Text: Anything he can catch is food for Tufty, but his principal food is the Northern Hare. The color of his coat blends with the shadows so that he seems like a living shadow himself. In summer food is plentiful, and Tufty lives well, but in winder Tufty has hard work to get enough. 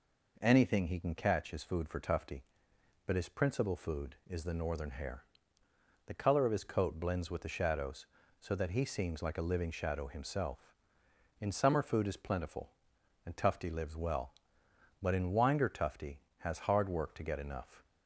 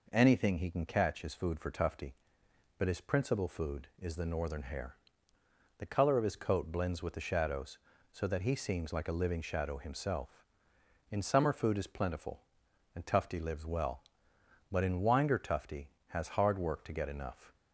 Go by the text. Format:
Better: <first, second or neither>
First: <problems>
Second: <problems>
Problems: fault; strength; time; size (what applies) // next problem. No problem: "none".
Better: neither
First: none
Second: none